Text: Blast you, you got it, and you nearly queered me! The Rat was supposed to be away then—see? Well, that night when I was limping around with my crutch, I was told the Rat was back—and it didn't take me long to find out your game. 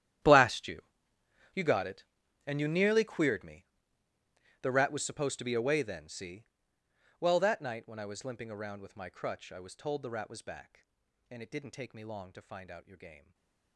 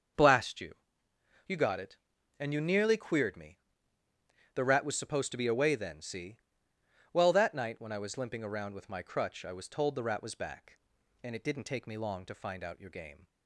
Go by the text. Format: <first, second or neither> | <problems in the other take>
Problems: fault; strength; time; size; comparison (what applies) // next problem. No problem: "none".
second | gets quieter; strong; throughout; 21 dB // starts louder than the rest; strong; until 1.9 s; 11.5 dB; also in the second // stays silent after the last word; slight; from 13.1 s on; 0.6 s long